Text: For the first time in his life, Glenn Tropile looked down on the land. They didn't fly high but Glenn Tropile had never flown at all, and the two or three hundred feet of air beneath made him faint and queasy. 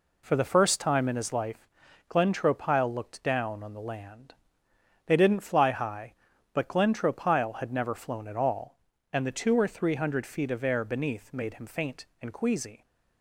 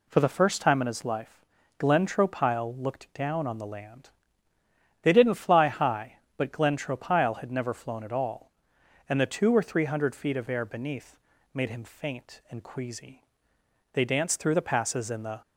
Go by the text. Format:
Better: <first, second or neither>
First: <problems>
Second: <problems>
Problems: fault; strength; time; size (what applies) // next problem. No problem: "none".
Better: first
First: none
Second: pauses between "beneath" and "made"; slight; at 11.1 s; 0.36 s long // goes on to say "They danced through the passes in the"; from 13.9 s on; 1.5 s long